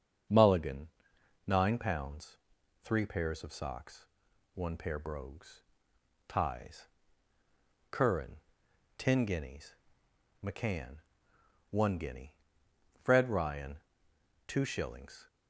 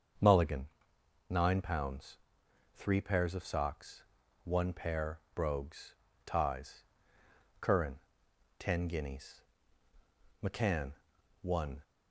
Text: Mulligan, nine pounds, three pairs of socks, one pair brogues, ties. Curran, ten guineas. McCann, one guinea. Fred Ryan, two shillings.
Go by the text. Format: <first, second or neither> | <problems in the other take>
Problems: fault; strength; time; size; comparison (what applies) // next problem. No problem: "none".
first | starts louder than the rest; until 1.8 s; 6.5 dB; also in the first // pauses between "pair" and "brogues"; slight; at 5.1 s; 0.16 s long // stops before "guinea Fred Ryan two shillings"; at 11.8 s